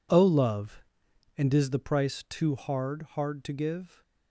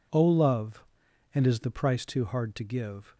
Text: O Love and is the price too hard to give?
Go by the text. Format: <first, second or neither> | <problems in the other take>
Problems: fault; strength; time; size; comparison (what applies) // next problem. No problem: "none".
second | says "hard" twice; at 3.1 s